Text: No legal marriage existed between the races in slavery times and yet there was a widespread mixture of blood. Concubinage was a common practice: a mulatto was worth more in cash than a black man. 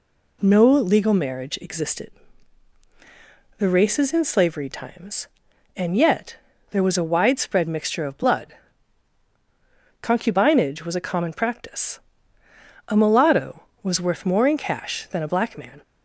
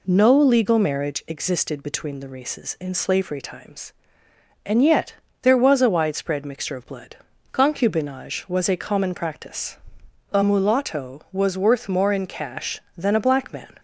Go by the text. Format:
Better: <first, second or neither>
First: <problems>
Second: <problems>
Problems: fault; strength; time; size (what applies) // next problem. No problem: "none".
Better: second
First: skips "between"; at 2.8 s // pauses between "yet" and "there"; slight; at 6.3 s; 0.34 s long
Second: pauses between "yet" and "there"; slight; at 5.1 s; 0.28 s long